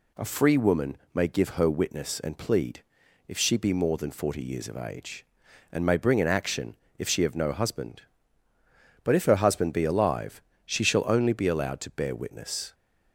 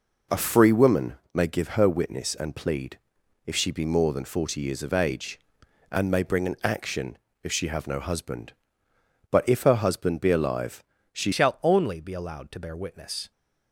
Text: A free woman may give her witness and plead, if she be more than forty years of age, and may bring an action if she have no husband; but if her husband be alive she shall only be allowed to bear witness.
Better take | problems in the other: first | pauses between "woman" and "may"; slight; at 1.1 s; 0.20 s long; slight in the first // pauses between "action" and "if"; slight; at 7.1 s; 0.24 s long; slight in the first // pauses between "alive" and "she"; slight; at 10.8 s; 0.28 s long; slight in the first // changes voice at "shall"; from 11.3 s on; 2.0 s long

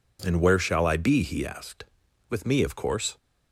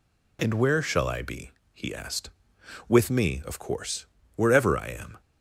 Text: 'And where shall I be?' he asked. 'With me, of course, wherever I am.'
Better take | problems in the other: second | stops before "wherever I am"; at 3.1 s

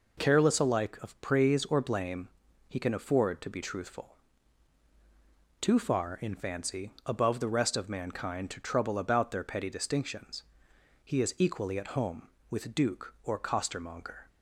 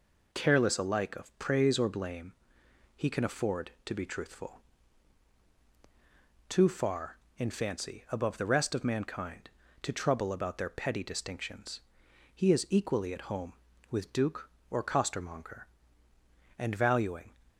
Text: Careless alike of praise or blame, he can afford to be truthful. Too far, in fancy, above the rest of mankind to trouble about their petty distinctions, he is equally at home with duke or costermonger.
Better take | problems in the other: first | goes on to say "And valuing"; noticeable; from 16.5 s on; 0.74 s long

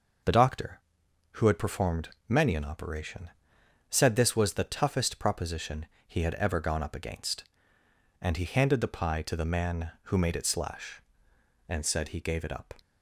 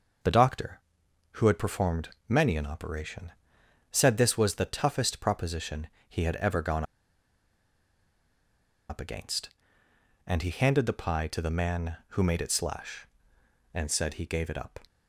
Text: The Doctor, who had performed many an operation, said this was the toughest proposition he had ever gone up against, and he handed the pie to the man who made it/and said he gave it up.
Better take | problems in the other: first | pauses between "performed" and "many"; slight; at 2.0 s; 0.20 s long; slight in the first // pauses between "proposition" and "he"; slight; at 5.8 s; 0.20 s long; slight in the first // pauses between "gone" and "up"; strong; at 6.8 s; 2.0 s long

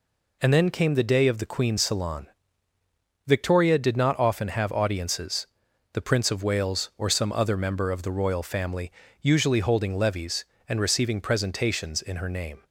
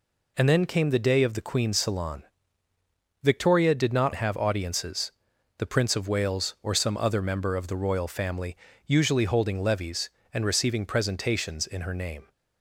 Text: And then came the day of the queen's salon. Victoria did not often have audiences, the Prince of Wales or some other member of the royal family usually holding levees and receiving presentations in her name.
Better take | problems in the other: first | skips "often"; at 4.1 s // pauses between "family" and "usually"; slight; at 8.5 s; 0.30 s long; slight in the first

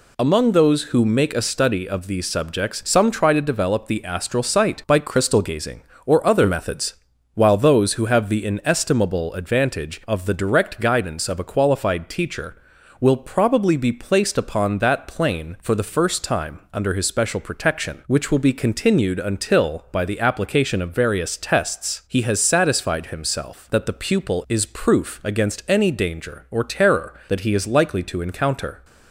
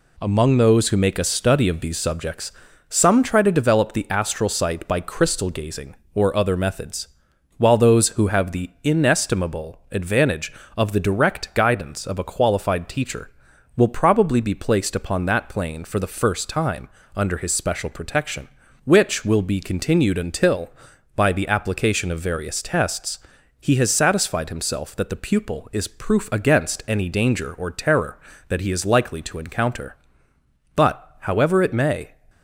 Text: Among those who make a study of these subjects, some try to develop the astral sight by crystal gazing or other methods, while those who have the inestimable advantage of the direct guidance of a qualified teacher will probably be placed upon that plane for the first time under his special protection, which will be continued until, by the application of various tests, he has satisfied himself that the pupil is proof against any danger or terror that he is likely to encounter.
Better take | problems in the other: first | pauses between "time" and "under"; slight; at 16.8 s; 0.28 s long // goes on to say "But however it may"; from 30.7 s on; 1.3 s long

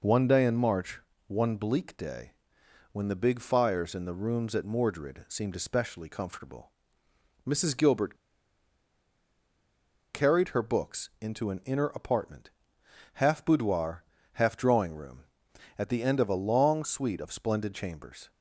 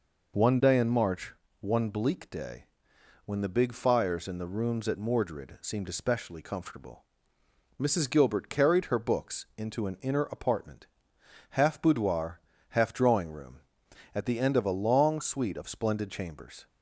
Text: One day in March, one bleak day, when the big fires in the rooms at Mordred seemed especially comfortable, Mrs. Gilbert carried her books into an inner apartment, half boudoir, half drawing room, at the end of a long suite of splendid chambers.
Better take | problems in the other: second | pauses between "Gilbert" and "carried"; strong; at 8.1 s; 1.9 s long

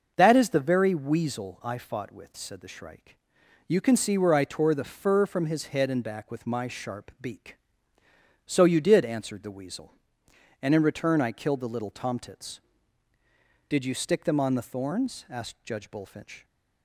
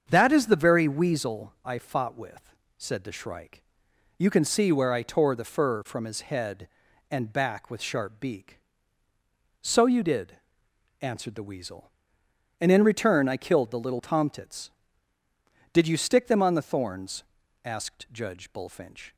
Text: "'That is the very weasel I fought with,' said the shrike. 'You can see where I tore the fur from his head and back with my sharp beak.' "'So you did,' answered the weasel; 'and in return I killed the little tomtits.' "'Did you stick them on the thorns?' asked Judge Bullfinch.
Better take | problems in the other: first | starts louder than the rest; strong; until 1.0 s; 7 dB // skips "my"; at 7.8 s

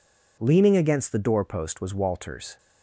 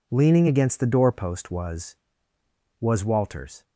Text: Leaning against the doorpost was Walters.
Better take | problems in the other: first | says "was" twice; at 2.8 s

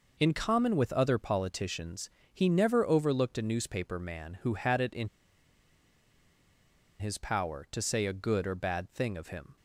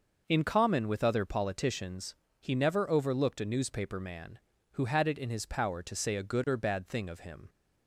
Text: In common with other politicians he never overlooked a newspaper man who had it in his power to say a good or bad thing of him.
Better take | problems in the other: second | pauses between "politicians" and "he"; slight; at 2.0 s; 0.24 s long; slight in the second // pauses between "in" and "his"; strong; at 5.0 s; 1.9 s long

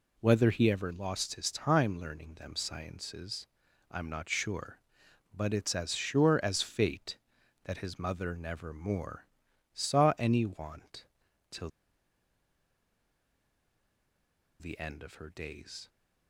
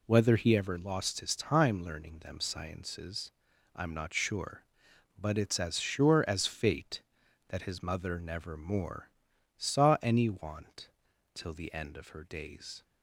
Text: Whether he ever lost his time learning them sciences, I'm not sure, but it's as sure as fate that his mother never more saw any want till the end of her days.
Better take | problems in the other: second | pauses between "more" and "saw"; noticeable; at 9.2 s; 0.46 s long; noticeable in the second // pauses between "want" and "till"; noticeable; at 11.0 s; 0.46 s long; noticeable in the second // pauses between "till" and "the"; strong; at 11.6 s; 2.9 s long

